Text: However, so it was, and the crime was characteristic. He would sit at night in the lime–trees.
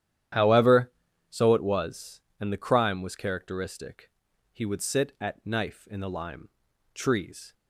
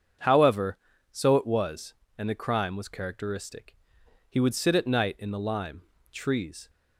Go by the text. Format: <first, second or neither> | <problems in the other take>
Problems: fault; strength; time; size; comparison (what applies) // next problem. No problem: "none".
second | starts louder than the rest; strong; until 1.7 s; 11 dB; also in the second // says "knife" for "night"; at 5.4 s